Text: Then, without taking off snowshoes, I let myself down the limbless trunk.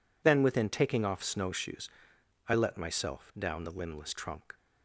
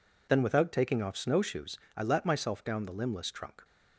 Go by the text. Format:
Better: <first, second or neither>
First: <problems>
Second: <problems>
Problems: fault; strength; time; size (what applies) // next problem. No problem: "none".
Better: second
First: says "within" for "without"; at 0.4 s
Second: none